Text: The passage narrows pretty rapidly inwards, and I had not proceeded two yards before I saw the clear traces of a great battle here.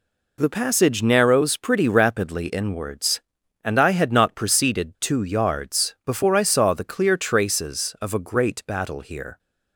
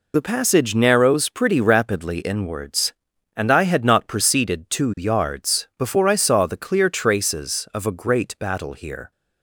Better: first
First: none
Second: loses the start of "The"; at 0.1 s; 40 ms

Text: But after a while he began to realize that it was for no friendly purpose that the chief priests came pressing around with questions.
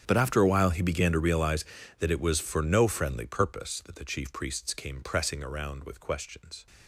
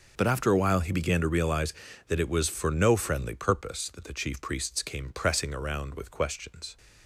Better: second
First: gets quieter; strong; throughout; 19.5 dB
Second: none

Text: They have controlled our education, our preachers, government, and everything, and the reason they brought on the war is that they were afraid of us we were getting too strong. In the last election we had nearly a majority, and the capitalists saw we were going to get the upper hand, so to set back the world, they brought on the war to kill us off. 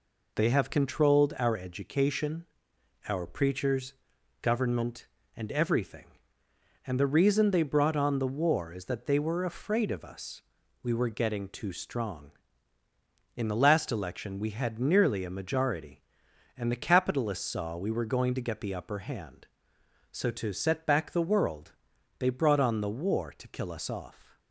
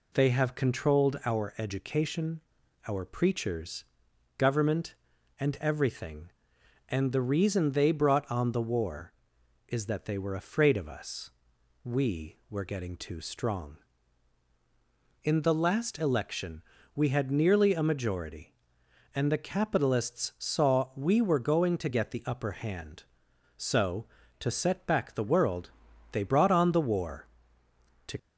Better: first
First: pauses between "us" and "we"; at 10.4 s; 0.40 s long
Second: pauses between "us" and "we"; noticeable; at 11.3 s; 0.54 s long // pauses between "election" and "we"; slight; at 16.6 s; 0.32 s long // stops before "kill us off"; at 28.1 s

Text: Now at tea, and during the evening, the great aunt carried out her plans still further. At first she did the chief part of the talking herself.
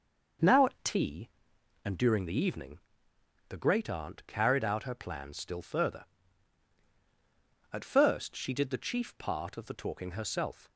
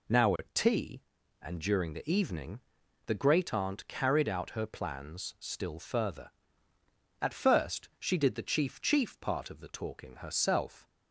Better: first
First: none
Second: says "chief" twice; at 8.7 s

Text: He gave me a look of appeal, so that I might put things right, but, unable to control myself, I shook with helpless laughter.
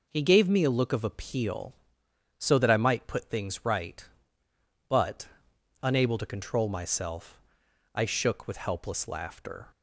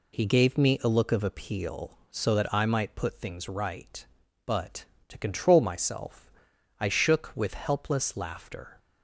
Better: first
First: none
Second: skips "unable"; at 4.9 s

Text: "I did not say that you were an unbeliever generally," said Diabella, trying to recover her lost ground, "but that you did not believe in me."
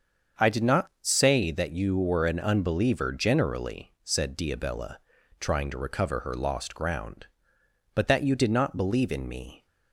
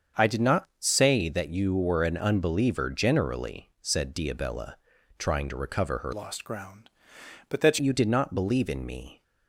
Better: first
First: starts louder than the rest; until 1.5 s; 7 dB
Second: starts louder than the rest; until 1.2 s; 7 dB // changes voice from "lost" to "that"; from 6.1 to 7.7 s; 1.6 s long

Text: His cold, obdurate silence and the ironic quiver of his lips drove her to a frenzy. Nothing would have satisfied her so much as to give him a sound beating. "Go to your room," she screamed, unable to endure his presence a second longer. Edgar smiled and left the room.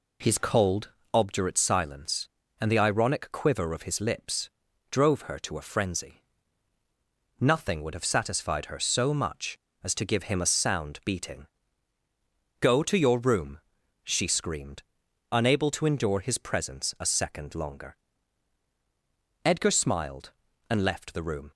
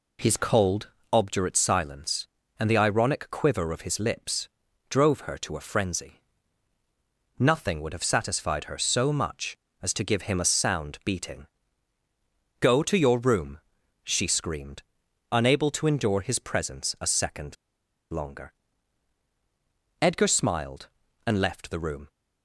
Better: first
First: pauses between "lips" and "drove"; at 4.5 s; 0.40 s long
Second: pauses between "lips" and "drove"; at 4.4 s; 0.40 s long // pauses between "second" and "longer"; noticeable; at 17.5 s; 0.56 s long

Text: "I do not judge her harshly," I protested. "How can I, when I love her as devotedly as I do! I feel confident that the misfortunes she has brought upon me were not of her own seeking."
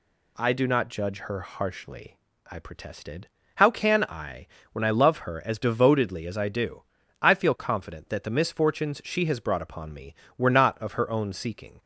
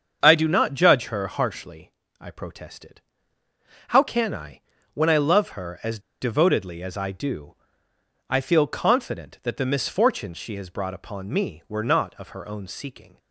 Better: first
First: none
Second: starts louder than the rest; until 1.2 s; 7 dB // pauses between "as" and "devotedly"; slight; at 5.9 s; 0.22 s long

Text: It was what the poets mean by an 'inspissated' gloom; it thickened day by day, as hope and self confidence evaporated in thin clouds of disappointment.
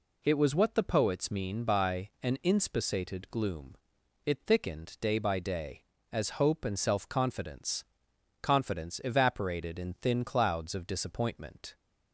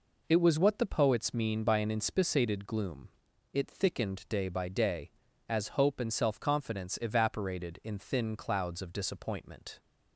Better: second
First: says "confidence" twice; at 8.4 s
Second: none

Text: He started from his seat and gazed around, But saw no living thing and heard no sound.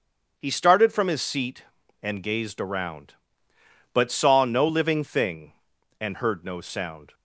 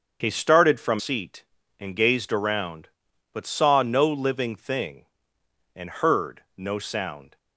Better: first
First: starts louder than the rest; until 1.3 s; 7 dB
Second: starts louder than the rest; until 1.2 s; 7 dB // skips "his"; at 0.9 s

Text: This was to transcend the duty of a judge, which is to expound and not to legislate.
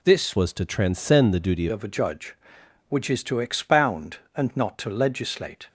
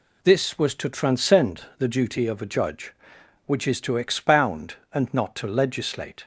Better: second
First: changes voice from "was" to "duty"; from 0.3 to 1.6 s; 1.3 s long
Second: none

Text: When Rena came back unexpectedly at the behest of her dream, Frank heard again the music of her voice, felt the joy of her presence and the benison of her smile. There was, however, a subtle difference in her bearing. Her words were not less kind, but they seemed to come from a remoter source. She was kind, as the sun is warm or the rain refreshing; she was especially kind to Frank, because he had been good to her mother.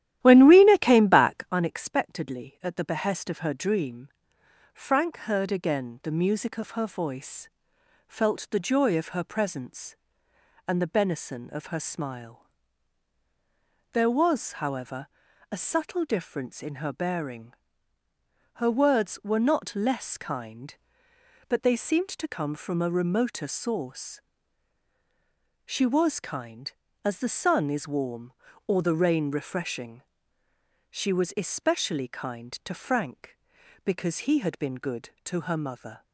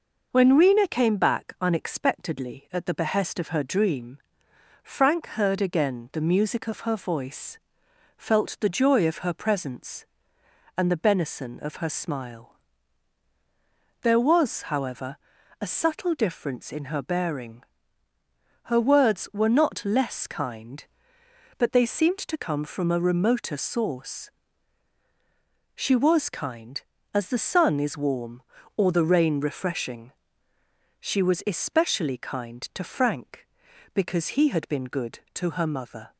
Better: second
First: starts louder than the rest; strong; until 1.6 s; 12.5 dB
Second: none

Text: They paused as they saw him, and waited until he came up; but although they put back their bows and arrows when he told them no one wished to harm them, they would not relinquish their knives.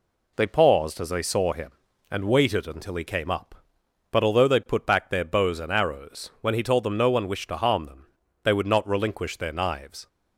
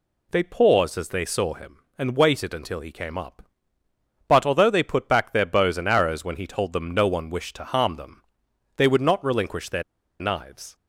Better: first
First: none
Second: pauses between "their" and "knives"; at 9.8 s; 0.37 s long

